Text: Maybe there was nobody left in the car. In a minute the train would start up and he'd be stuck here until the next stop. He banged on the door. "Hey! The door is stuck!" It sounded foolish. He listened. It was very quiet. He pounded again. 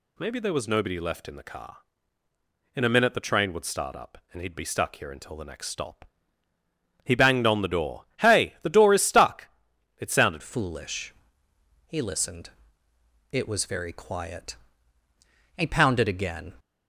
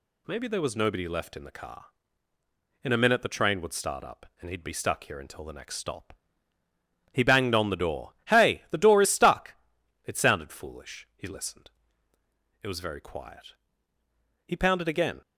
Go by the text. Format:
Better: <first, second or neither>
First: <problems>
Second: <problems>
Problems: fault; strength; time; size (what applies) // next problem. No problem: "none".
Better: second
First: changes voice at "foolish"; from 10.4 s on; 6.1 s long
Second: none